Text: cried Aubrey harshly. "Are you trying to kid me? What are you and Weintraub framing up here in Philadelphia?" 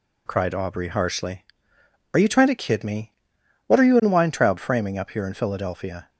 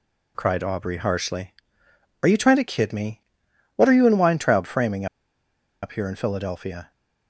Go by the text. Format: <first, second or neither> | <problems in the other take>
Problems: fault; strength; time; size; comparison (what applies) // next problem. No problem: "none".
first | pauses between "framing" and "up"; noticeable; at 5.0 s; 0.76 s long